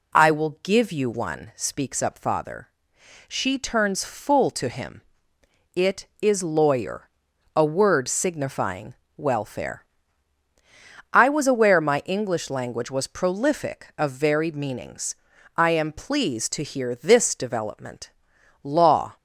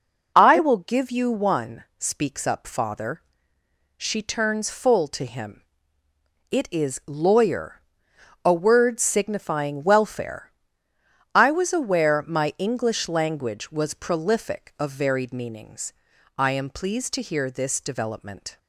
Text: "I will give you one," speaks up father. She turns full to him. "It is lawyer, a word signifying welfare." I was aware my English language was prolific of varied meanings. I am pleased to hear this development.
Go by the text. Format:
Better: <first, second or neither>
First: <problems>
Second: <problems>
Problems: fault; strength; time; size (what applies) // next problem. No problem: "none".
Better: second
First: pauses between "signifying" and "welfare"; slight; at 8.9 s; 0.24 s long // goes on to say "Law"; from 18.6 s on; 0.54 s long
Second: none